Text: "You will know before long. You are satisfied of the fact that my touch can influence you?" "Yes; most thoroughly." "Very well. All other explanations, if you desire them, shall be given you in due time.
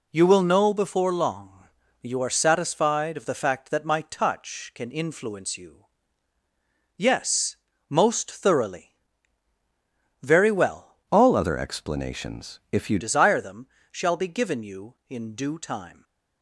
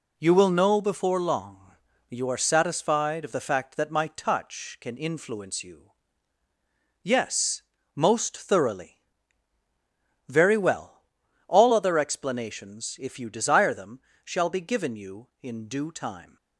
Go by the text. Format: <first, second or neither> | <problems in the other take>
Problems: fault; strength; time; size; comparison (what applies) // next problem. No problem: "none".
second | changes voice from "All" to "you"; from 11.1 to 12.9 s; 1.8 s long